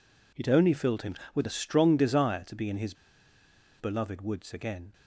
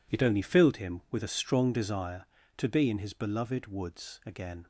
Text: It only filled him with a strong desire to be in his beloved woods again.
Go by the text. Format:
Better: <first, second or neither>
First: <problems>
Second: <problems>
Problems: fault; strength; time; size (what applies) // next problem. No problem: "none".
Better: second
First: pauses between "his" and "beloved"; noticeable; at 2.9 s; 0.85 s long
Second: none